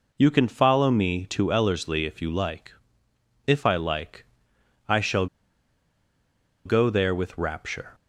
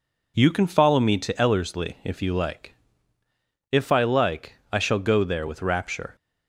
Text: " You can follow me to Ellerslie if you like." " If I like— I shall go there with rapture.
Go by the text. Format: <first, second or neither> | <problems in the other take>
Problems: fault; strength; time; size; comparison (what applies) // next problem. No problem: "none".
second | pauses between "shall" and "go"; strong; at 5.2 s; 1.3 s long